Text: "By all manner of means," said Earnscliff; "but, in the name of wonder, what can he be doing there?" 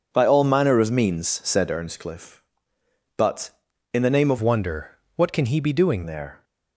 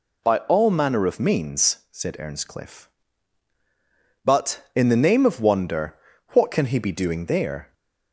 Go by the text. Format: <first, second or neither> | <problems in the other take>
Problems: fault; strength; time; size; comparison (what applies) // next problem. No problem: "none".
second | changes voice from "wonder" to "doing"; from 4.3 to 6.0 s; 1.7 s long